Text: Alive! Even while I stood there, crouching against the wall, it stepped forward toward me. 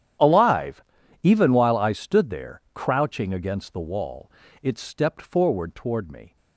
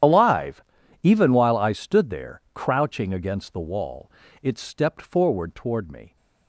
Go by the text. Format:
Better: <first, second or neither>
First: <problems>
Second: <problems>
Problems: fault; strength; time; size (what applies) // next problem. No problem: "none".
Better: first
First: starts louder than the rest; strong; until 1.6 s; 10 dB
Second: loses the start of "Alive"; at 0.0 s; 30 ms // starts louder than the rest; strong; until 1.4 s; 10 dB